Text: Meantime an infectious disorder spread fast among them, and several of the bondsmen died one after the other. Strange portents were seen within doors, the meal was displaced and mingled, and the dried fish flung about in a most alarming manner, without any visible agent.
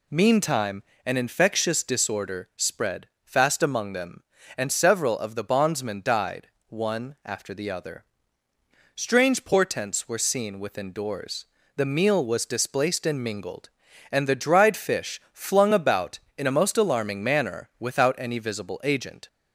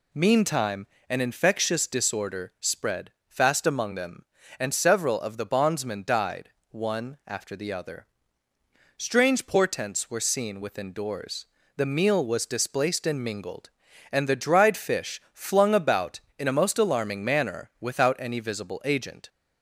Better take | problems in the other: neither | pauses between "Meantime" and "an"; slight; the same in both // pauses between "spread" and "fast"; slight; the same in both // pauses between "died" and "one"; slight; the same in both

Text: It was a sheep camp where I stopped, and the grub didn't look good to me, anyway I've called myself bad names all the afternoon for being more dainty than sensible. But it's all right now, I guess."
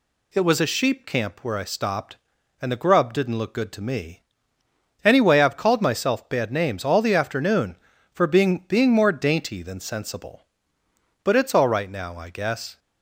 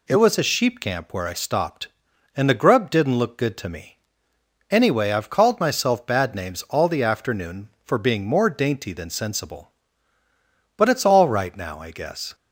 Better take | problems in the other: second | says "being" twice; at 8.6 s

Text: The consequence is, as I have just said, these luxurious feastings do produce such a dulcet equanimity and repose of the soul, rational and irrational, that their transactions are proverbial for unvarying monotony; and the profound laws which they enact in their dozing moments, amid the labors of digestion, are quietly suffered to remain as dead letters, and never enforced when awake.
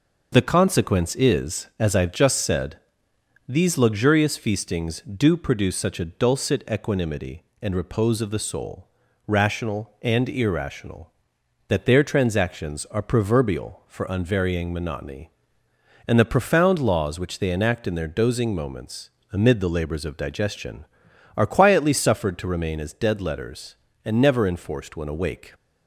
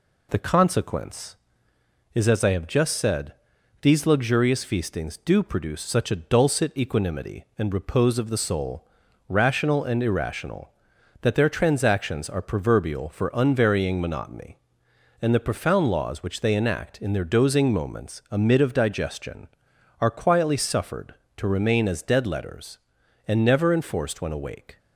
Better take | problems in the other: first | skips "the labors"; at 18.5 s

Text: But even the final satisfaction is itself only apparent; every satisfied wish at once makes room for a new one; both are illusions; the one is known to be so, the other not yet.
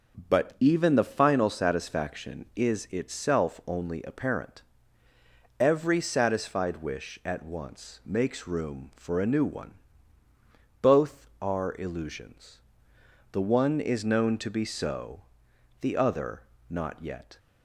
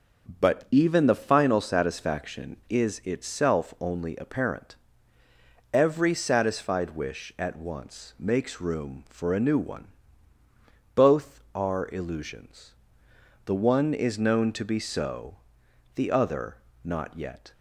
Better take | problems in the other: neither | starts louder than the rest; the same in both // pauses between "other" and "not"; slight; the same in both

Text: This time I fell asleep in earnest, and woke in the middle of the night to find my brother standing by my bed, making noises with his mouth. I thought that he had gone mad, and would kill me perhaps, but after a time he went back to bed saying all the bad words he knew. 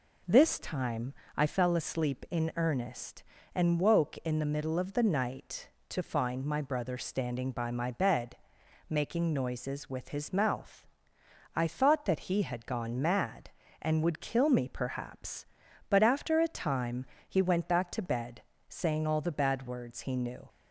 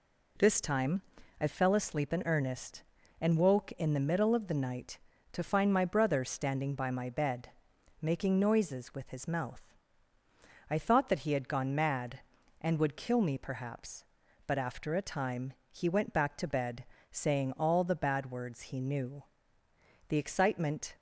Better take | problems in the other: first | pauses between "time" and "I"; at 1.0 s; 0.40 s long; slight in the first // pauses between "time" and "he"; slight; at 15.5 s; 0.18 s long; slight in the first // pauses between "bed" and "saying"; slight; at 16.8 s; 0.26 s long; slight in the first // goes on to say "The excitement"; noticeable; from 20.0 s on; 0.88 s long

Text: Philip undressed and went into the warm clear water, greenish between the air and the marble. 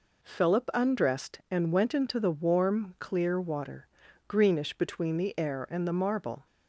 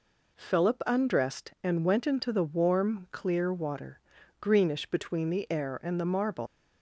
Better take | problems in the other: first | leaves "marble" unfinished; at 6.4 s; 115 ms

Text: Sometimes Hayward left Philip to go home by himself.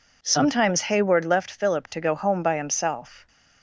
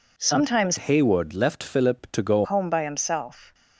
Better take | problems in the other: first | changes voice from "Hayward" to "go"; from 0.7 to 2.4 s; 1.7 s long

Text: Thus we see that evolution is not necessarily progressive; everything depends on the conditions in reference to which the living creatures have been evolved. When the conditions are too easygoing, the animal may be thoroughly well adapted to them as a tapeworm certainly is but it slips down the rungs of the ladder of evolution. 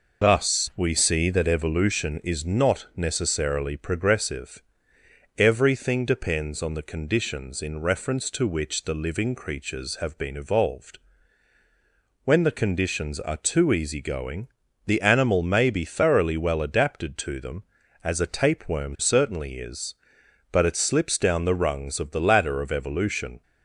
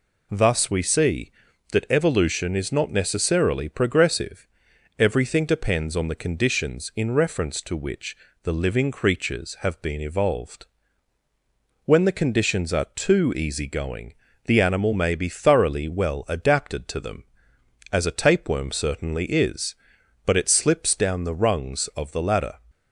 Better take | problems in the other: first | pauses between "which" and "the"; slight; at 8.1 s; 0.26 s long // stops before "of evolution"; at 22.6 s

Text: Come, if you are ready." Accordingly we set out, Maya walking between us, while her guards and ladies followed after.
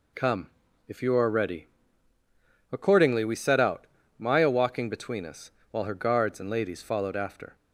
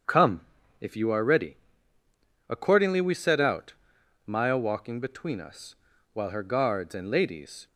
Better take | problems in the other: first | starts louder than the rest; strong; until 1.4 s; 7.5 dB // stops before "followed after"; at 7.6 s

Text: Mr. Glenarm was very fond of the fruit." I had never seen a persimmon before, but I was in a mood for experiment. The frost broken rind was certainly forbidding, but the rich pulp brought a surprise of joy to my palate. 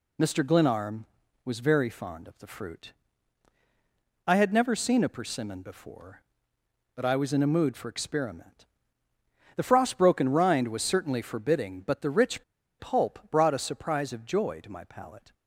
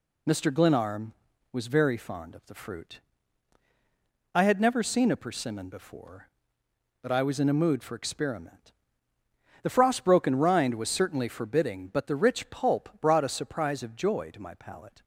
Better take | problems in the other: second | pauses between "rich" and "pulp"; slight; at 12.4 s; 0.35 s long

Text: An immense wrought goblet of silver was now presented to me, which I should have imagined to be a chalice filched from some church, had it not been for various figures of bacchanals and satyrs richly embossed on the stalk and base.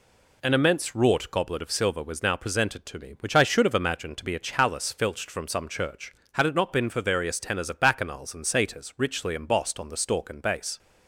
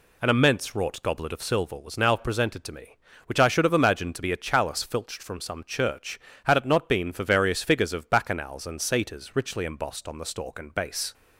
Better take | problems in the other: second | says "tenors" for "figures"; at 7.3 s

